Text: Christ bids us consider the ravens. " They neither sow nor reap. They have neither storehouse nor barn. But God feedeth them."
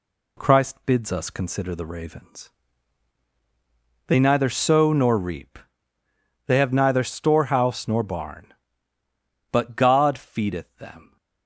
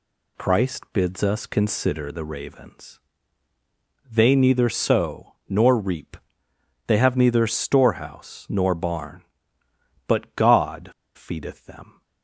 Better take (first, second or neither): first